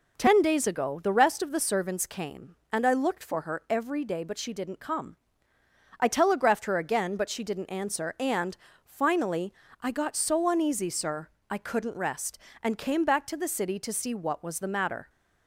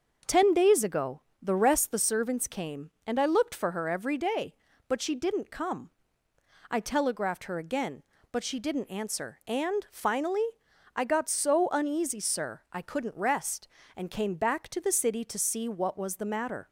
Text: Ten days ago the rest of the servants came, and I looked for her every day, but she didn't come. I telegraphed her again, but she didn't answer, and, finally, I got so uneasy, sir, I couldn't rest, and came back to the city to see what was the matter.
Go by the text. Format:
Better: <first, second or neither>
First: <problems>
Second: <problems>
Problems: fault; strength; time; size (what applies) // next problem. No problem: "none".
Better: first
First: none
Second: starts louder than the rest; until 1.4 s; 6.5 dB // pauses between "ago" and "the"; slight; at 1.2 s; 0.22 s long // skips "of"; at 1.9 s